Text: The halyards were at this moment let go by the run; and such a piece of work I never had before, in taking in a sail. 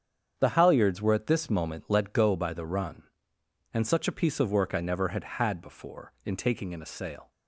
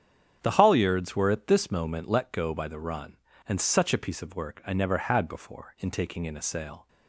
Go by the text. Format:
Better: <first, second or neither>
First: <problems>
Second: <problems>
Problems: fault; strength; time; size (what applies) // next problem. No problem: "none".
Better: second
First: starts louder than the rest; strong; until 1.3 s; 8 dB // says "had" twice; at 5.2 s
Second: starts louder than the rest; strong; until 1.4 s; 8.5 dB